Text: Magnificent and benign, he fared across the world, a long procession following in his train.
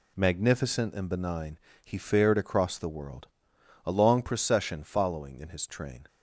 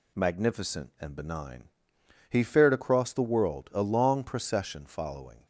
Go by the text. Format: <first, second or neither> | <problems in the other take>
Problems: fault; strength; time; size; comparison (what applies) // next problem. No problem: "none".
first | stops before "in his train"; at 5.4 s